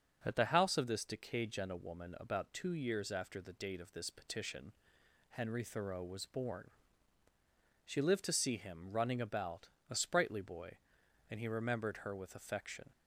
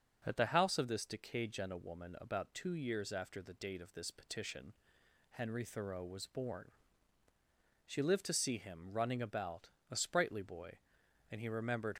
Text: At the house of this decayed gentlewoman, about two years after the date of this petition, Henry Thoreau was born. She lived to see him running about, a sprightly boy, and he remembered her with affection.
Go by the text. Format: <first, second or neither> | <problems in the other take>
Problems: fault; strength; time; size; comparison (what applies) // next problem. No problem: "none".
first | stops before "her with affection"; at 11.9 s